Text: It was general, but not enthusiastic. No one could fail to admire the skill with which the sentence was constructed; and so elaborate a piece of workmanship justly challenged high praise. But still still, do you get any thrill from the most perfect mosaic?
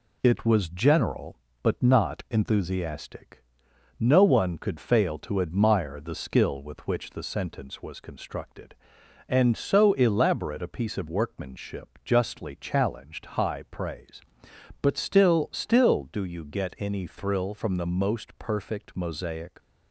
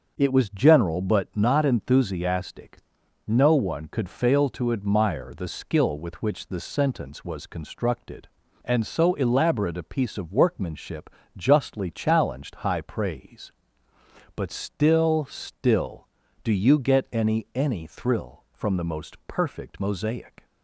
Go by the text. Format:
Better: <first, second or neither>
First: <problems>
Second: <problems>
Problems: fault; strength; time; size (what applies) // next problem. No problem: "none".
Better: first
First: none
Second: starts louder than the rest; until 1.1 s; 6 dB // pauses between "workmanship" and "justly"; slight; at 11.1 s; 0.26 s long // says "any" twice; at 17.5 s